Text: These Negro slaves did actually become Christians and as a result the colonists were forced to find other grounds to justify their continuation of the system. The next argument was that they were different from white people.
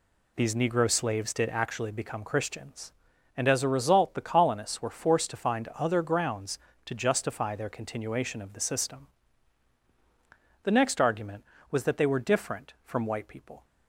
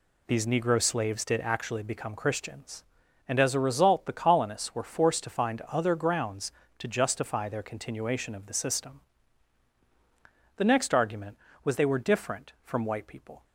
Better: first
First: none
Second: skips "that"; at 11.7 s

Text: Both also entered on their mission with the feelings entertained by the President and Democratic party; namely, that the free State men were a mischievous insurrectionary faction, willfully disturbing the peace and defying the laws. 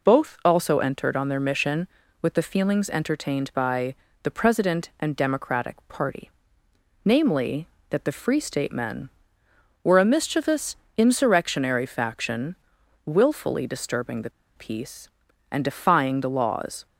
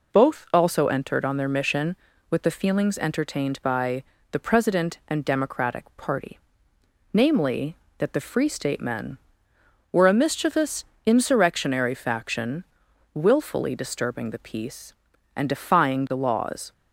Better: second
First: pauses between "by" and "the"; slight; at 3.9 s; 0.28 s long // pauses between "mischievous" and "insurrectionary"; slight; at 10.7 s; 0.22 s long // pauses between "the" and "peace"; slight; at 14.2 s; 0.26 s long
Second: pauses between "by" and "the"; slight; at 4.0 s; 0.28 s long // pauses between "mischievous" and "insurrectionary"; slight; at 10.8 s; 0.22 s long

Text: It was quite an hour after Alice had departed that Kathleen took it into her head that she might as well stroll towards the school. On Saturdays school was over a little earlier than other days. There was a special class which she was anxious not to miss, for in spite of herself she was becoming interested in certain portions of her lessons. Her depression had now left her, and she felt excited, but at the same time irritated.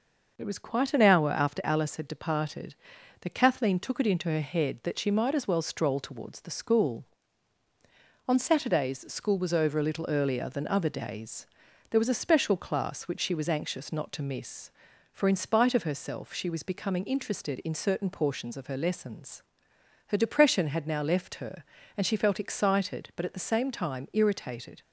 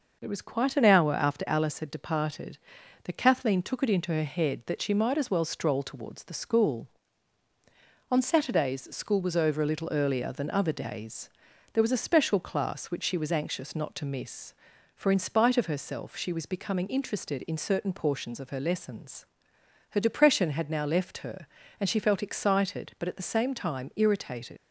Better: first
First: none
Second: leaves "irritated" unfinished; at 24.5 s; 80 ms

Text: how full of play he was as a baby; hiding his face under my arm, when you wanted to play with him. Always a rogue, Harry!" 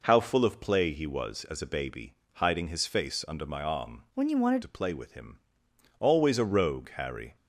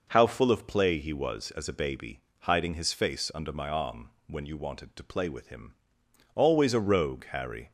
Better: second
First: changes voice from "when" to "wanted"; from 4.1 to 4.6 s; 0.5 s long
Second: none

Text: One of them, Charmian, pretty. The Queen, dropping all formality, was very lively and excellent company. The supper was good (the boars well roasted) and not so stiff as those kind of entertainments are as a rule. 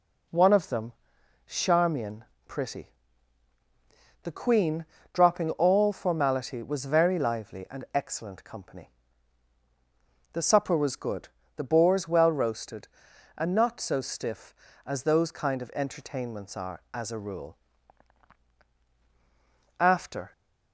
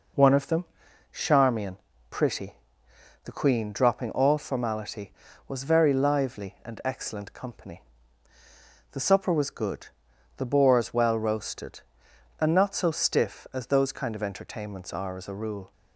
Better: second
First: goes on to say "After"; from 19.7 s on; 0.52 s long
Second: none

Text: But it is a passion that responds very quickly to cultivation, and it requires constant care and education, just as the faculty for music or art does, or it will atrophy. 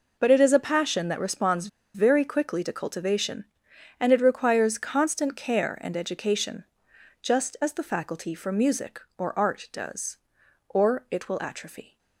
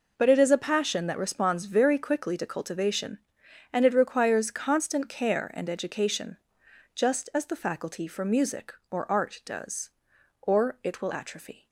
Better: second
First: pauses between "responds" and "very"; slight; at 1.6 s; 0.27 s long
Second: none

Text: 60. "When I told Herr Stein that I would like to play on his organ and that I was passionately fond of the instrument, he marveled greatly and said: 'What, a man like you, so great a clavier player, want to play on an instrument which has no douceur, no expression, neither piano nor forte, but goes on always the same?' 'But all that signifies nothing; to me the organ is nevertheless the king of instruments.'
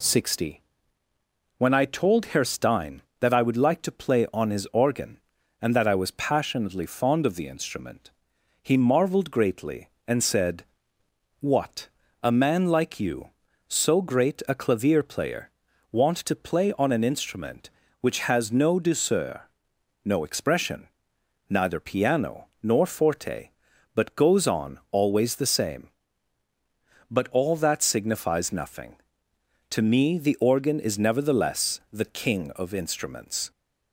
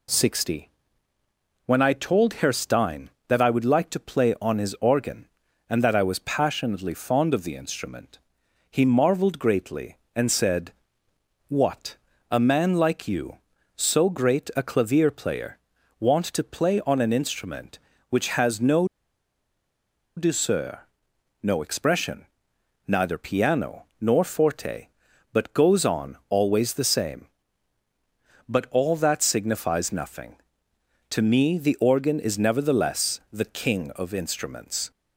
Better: first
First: pauses between "piano" and "nor"; slight; at 22.4 s; 0.16 s long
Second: pauses between "no" and "douceur"; strong; at 18.8 s; 1.2 s long // pauses between "piano" and "nor"; slight; at 23.8 s; 0.16 s long

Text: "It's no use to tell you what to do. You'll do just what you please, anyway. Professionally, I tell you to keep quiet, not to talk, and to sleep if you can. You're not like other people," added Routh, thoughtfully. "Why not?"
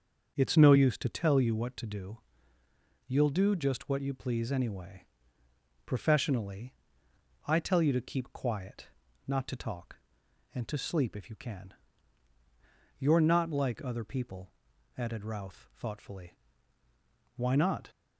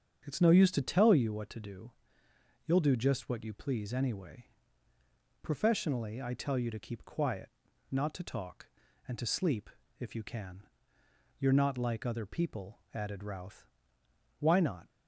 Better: first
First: starts louder than the rest; until 1.3 s; 6.5 dB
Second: starts louder than the rest; strong; until 1.2 s; 7.5 dB // pauses between "sleep" and "if"; slight; at 9.6 s; 0.31 s long // skips "thoughtfully"; at 14.0 s

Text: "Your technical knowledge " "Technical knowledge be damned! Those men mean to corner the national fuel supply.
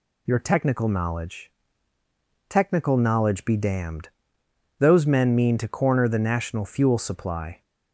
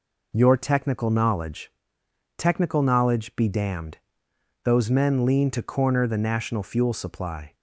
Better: first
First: none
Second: says "lean" for "mean"; at 5.2 s

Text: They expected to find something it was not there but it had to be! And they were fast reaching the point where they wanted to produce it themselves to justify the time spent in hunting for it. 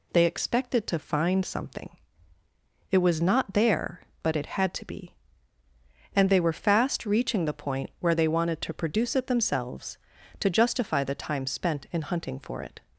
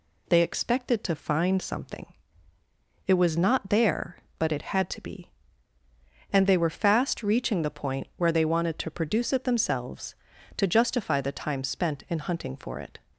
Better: neither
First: pauses between "something" and "it"; at 1.8 s; 1.0 s long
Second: pauses between "something" and "it"; at 2.0 s; 0.99 s long

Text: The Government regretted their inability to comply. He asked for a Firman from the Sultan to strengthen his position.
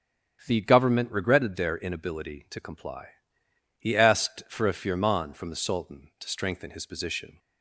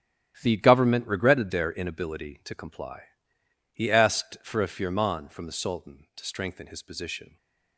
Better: first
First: starts louder than the rest; strong; until 1.4 s; 8.5 dB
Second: gets quieter; strong; throughout; 11.5 dB // starts louder than the rest; strong; until 1.4 s; 11.5 dB

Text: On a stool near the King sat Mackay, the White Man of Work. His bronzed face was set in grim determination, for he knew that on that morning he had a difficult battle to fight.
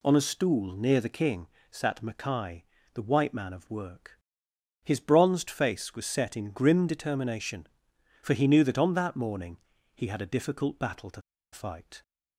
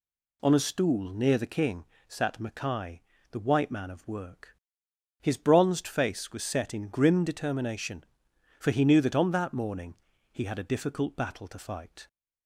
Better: second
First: pauses between "King" and "sat"; slight; at 1.4 s; 0.24 s long // pauses between "morning" and "he"; at 9.5 s; 0.38 s long // pauses between "to" and "fight"; slight; at 11.2 s; 0.31 s long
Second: pauses between "King" and "sat"; slight; at 1.8 s; 0.24 s long // pauses between "morning" and "he"; at 9.9 s; 0.38 s long

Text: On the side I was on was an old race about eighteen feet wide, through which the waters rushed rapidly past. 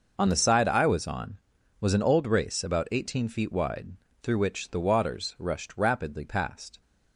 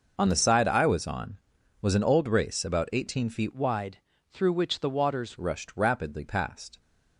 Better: first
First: none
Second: changes voice from "wide" to "waters"; from 3.5 to 5.3 s; 1.8 s long

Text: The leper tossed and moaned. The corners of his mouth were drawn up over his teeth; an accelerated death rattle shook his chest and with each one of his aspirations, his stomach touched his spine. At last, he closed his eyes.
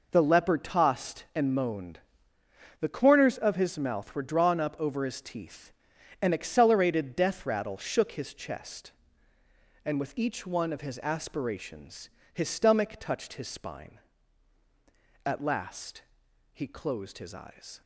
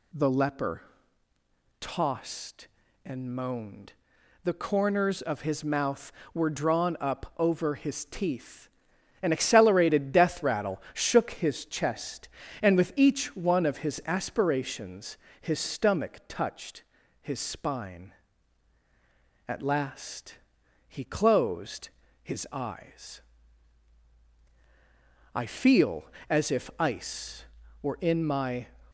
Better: first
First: none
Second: pauses between "leper" and "tossed"; noticeable; at 0.8 s; 0.98 s long // pauses between "touched" and "his"; at 16.8 s; 0.40 s long // pauses between "closed" and "his"; slight; at 21.8 s; 0.34 s long // goes on to say "I feel as if ice were in my"; strong; from 25.3 s on; 3.3 s long

